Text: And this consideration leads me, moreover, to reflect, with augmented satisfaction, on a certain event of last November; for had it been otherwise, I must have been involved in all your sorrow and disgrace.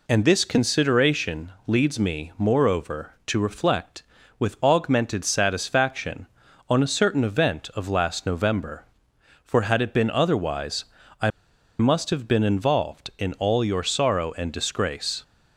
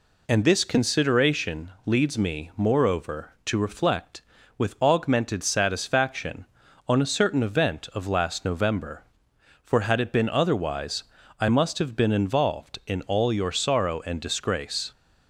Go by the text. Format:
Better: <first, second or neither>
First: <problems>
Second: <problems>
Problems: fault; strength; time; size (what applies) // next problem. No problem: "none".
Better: second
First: pauses between "I" and "must"; noticeable; at 11.2 s; 0.49 s long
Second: none